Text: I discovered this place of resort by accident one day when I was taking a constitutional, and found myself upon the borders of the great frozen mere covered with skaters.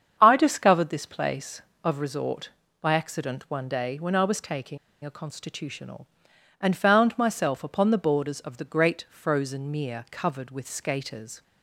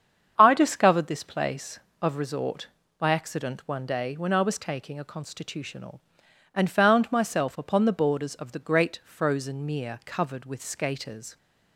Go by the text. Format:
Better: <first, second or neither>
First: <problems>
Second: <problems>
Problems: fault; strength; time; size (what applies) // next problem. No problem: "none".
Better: second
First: starts louder than the rest; strong; until 1.2 s; 7.5 dB // pauses between "taking" and "a"; slight; at 4.7 s; 0.26 s long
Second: starts louder than the rest; strong; until 1.3 s; 7.5 dB